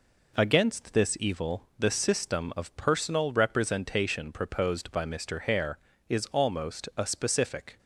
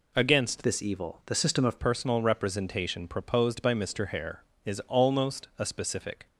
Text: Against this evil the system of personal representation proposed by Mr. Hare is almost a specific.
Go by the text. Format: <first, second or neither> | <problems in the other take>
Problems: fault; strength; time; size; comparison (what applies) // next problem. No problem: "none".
first | changes voice from "this" to "of"; from 0.6 to 1.7 s; 1.1 s long